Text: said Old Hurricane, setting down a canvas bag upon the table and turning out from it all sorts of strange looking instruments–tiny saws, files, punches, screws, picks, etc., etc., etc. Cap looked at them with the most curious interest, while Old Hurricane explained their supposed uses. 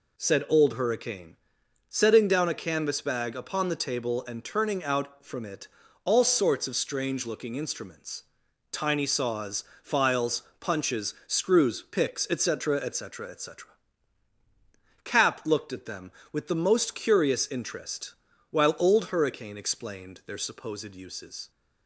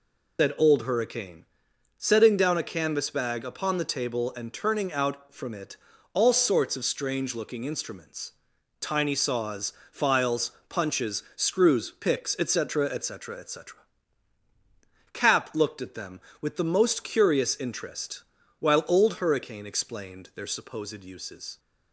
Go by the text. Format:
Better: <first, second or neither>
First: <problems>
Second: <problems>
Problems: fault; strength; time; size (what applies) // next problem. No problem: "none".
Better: first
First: pauses between "it" and "all"; slight; at 5.6 s; 0.36 s long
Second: loses the start of "said"; at 0.3 s; 125 ms // pauses between "it" and "all"; slight; at 5.7 s; 0.36 s long